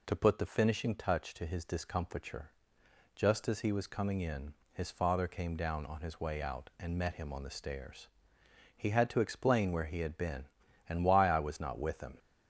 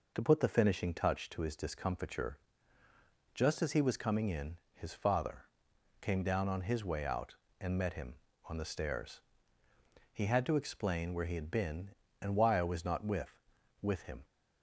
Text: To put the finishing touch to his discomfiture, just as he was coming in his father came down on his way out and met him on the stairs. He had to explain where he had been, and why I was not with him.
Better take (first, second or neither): first